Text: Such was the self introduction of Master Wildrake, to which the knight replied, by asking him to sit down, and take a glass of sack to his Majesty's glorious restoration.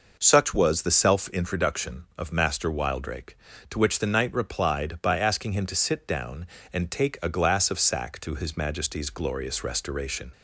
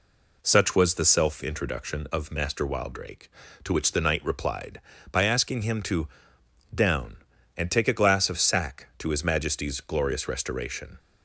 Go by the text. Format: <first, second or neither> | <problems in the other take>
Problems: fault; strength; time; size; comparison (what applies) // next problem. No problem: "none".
first | skips "sit"; at 6.4 s